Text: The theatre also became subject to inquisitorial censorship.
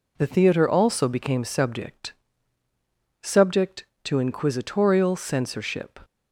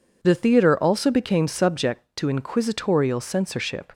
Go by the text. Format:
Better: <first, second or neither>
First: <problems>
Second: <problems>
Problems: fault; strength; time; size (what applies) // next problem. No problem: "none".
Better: second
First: says "subject" twice; at 3.2 s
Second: none